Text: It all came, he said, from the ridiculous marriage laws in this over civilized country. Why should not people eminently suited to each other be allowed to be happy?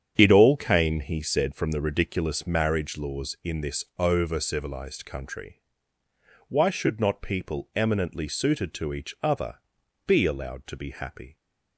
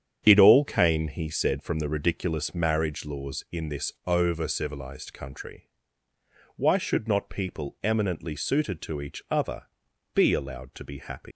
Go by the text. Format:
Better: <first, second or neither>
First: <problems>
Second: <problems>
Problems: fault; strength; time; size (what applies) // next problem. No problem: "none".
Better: first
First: starts louder than the rest; strong; until 1.1 s; 8.5 dB // pauses between "this" and "over"; slight; at 3.8 s; 0.16 s long // pauses between "other" and "be"; noticeable; at 9.5 s; 0.52 s long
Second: starts louder than the rest; strong; until 1.2 s; 8.5 dB // pauses between "this" and "over"; slight; at 3.9 s; 0.16 s long // pauses between "other" and "be"; noticeable; at 9.6 s; 0.52 s long // leaves "happy" unfinished; at 11.3 s; 140 ms